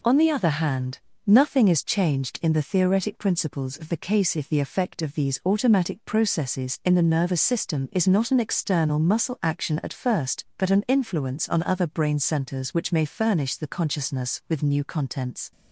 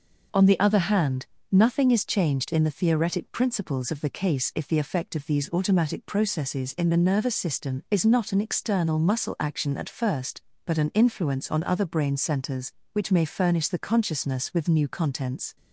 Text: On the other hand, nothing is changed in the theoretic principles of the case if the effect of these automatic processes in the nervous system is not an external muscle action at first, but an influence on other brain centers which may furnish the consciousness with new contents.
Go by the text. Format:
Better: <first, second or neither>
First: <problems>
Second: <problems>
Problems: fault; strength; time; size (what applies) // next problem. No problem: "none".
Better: neither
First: none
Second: none